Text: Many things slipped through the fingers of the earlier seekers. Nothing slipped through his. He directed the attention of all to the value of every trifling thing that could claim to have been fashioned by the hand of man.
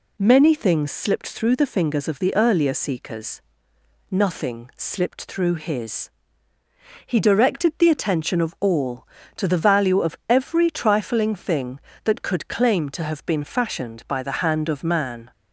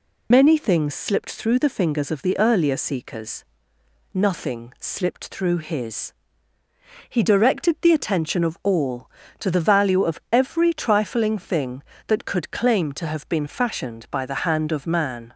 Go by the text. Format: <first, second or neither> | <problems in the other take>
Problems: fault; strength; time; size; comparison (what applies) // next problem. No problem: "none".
first | loses the start of "Many"; at 0.3 s; 85 ms